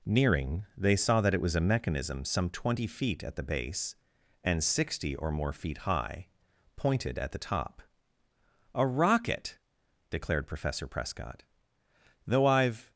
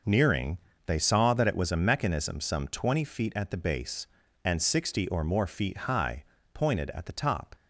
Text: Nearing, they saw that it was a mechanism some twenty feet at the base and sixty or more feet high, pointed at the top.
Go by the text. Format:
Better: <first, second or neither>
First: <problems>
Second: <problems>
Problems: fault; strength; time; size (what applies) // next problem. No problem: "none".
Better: second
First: goes on to say "A rocket declared Professor Prescott Though I've"; strong; from 8.7 s on; 4.1 s long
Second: none